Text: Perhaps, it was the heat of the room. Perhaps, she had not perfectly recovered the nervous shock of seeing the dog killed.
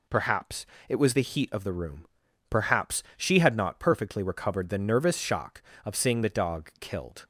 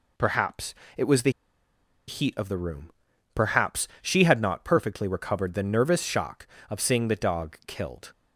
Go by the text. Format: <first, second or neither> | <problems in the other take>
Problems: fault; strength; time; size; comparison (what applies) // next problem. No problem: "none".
first | pauses between "the" and "heat"; noticeable; at 1.2 s; 0.78 s long